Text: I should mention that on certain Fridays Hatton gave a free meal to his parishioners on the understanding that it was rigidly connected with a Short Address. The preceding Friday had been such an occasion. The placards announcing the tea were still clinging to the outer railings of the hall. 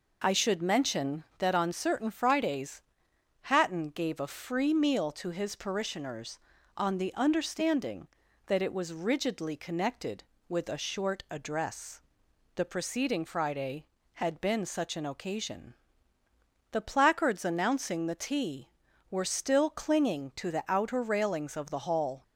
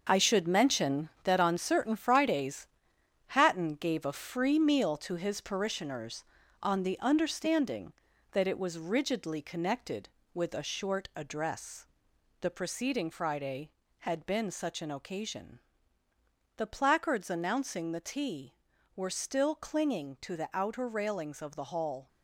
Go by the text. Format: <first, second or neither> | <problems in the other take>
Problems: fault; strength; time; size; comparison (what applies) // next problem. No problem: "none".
first | gets quieter; strong; throughout; 8 dB // pauses between "Fridays" and "Hatton"; noticeable; at 2.6 s; 0.62 s long; noticeable in the first